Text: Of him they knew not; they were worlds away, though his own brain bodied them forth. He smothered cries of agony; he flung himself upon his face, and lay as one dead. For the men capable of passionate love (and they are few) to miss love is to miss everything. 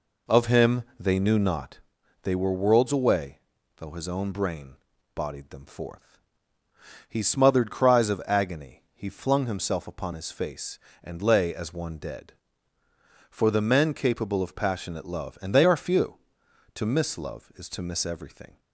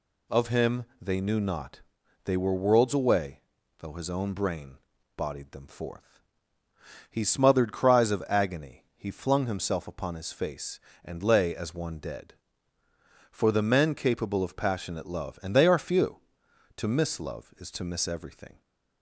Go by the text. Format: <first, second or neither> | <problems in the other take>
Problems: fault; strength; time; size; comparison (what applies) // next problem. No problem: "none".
second | starts louder than the rest; until 1.7 s; 3.5 dB // pauses between "him" and "they"; slight; at 0.8 s; 0.16 s long; slight in the second // pauses between "brain" and "bodied"; at 4.7 s; 0.40 s long; also in the second